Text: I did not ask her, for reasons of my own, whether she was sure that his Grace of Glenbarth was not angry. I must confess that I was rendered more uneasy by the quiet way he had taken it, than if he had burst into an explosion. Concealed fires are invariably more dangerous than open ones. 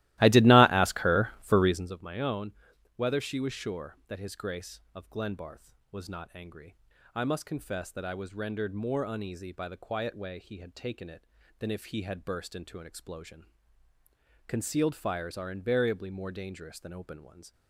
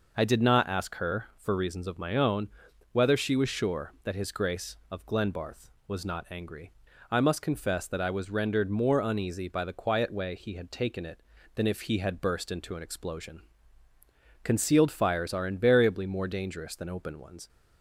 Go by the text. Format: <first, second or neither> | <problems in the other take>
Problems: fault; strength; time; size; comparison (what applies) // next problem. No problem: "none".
second | starts louder than the rest; strong; until 2.0 s; 17 dB